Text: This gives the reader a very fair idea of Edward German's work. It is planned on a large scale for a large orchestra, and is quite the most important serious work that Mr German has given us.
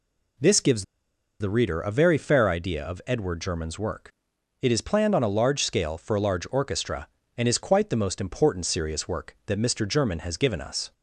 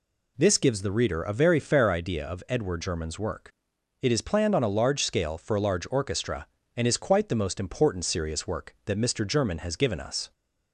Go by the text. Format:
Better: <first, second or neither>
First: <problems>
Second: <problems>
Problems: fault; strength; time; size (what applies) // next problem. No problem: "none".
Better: second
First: pauses between "gives" and "the"; noticeable; at 0.8 s; 0.55 s long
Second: none